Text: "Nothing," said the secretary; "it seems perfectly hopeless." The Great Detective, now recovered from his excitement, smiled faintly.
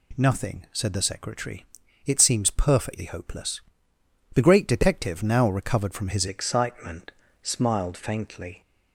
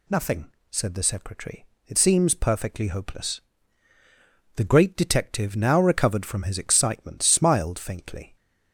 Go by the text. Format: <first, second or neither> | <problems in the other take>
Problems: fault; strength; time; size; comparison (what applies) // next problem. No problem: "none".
second | changes voice at "excitement"; from 6.2 s on; 2.4 s long